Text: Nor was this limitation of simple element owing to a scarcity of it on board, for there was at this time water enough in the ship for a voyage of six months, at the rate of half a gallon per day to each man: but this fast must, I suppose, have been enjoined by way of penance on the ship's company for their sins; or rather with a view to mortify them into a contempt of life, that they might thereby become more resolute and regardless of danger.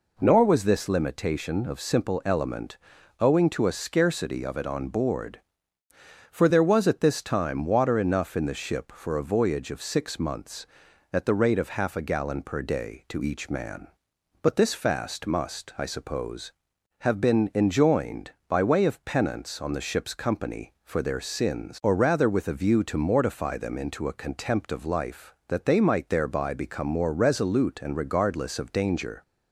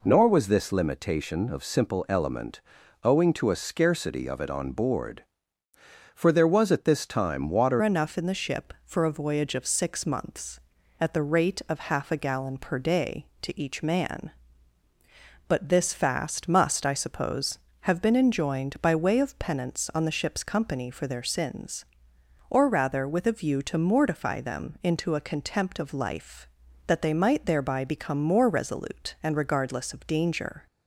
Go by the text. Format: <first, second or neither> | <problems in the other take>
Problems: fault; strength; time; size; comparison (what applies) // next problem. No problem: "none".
first | pauses between "element" and "owing"; at 2.6 s; 0.44 s long; also in the first // changes voice at "enough"; from 7.8 s on; 22.8 s long